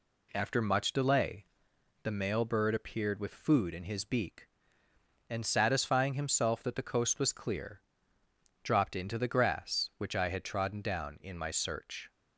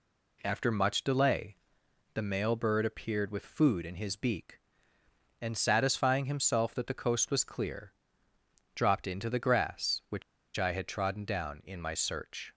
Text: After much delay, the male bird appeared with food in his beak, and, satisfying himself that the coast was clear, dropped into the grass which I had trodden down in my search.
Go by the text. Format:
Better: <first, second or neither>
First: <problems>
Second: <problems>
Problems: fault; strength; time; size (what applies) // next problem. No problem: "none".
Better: first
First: none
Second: pauses between "which" and "I"; slight; at 10.2 s; 0.34 s long